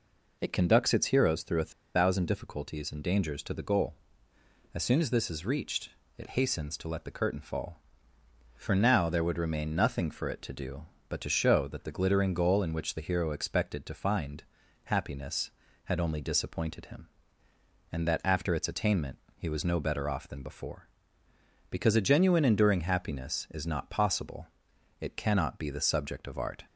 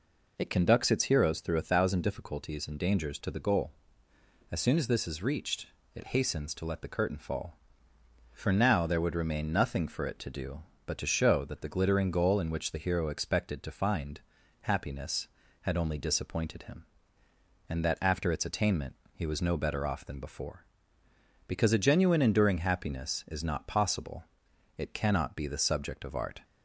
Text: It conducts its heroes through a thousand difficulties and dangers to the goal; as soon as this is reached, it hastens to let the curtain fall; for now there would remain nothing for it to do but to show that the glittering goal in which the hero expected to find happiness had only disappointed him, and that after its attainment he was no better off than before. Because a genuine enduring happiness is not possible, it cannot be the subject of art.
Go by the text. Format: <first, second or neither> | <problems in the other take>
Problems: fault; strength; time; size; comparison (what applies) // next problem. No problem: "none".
second | pauses between "a" and "thousand"; slight; at 1.7 s; 0.24 s long // pauses between "find" and "happiness"; at 14.4 s; 0.44 s long; also in the second // pauses between "attainment" and "he"; slight; at 19.1 s; 0.18 s long; slight in the second